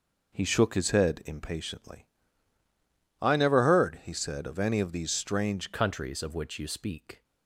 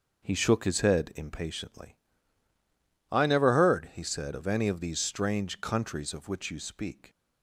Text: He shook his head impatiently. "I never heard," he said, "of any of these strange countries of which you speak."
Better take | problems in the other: second | changes voice at "countries"; from 5.7 s on; 1.5 s long

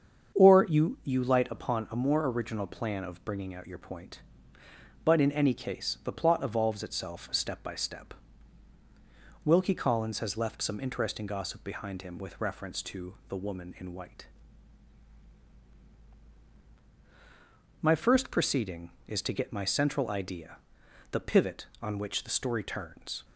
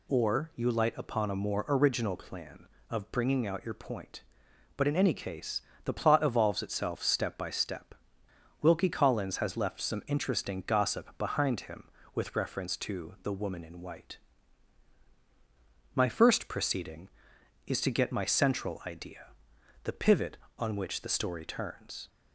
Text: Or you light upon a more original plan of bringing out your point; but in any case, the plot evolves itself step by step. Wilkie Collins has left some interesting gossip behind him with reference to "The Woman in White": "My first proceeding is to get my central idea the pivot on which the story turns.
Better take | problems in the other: second | starts louder than the rest; strong; until 1.4 s; 7 dB // says "you" twice; at 1.0 s // pauses between "idea" and "the"; noticeable; at 20.5 s; 0.54 s long; noticeable in the second

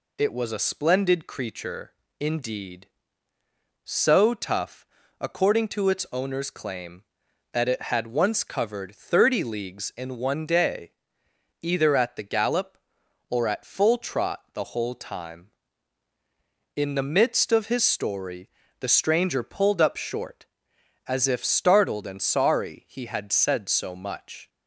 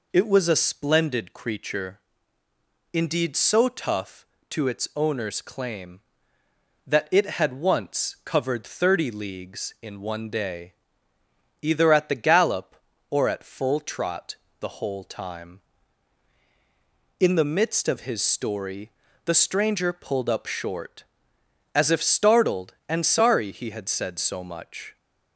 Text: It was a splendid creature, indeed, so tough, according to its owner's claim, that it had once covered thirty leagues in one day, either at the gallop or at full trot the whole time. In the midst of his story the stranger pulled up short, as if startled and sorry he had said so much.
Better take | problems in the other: first | skips "according"; at 4.3 s // pauses between "trot" and "the"; slight; at 14.3 s; 0.24 s long // pauses between "story" and "the"; slight; at 18.9 s; 0.32 s long; slight in the first

